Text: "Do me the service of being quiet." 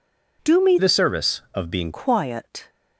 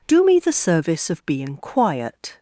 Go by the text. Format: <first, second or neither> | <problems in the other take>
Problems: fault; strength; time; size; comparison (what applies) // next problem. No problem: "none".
second | changes voice from "the" to "being"; from 0.7 to 1.9 s; 1.2 s long